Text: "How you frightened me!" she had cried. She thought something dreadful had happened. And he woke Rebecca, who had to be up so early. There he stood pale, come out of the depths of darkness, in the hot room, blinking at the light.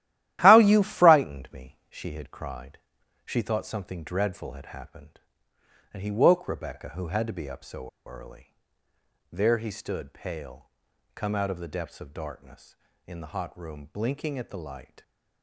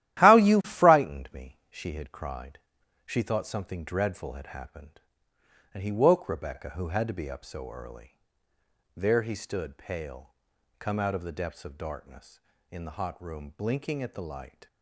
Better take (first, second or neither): second